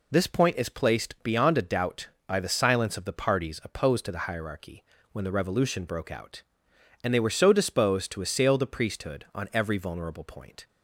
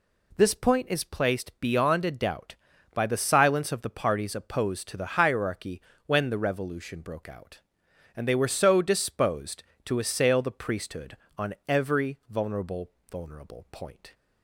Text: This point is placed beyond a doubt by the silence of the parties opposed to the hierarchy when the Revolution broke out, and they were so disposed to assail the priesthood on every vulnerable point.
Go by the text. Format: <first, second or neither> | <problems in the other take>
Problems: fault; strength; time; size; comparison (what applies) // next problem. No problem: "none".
first | pauses between "hierarchy" and "when"; slight; at 5.8 s; 0.24 s long; slight in the first // says "vulnerable" twice; at 13.0 s